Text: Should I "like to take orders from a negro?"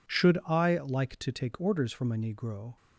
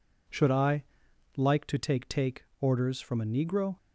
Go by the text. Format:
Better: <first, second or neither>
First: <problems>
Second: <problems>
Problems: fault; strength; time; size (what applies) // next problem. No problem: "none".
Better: first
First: none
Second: pauses between "I" and "like"; noticeable; at 0.8 s; 0.54 s long // says "take" twice; at 2.0 s